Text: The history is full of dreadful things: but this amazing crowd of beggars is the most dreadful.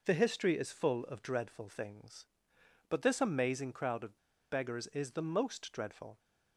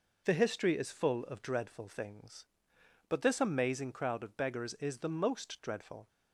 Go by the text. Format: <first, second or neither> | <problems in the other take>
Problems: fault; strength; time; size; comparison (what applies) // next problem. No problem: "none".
second | pauses between "of" and "beggars"; slight; at 4.1 s; 0.34 s long